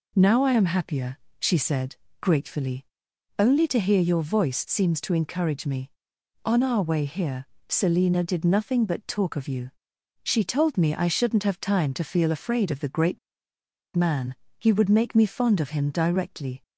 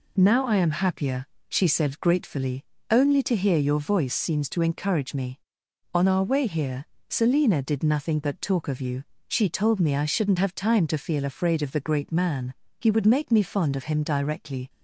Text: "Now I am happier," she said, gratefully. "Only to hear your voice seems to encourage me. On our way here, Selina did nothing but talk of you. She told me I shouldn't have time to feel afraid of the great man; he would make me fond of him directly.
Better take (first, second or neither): second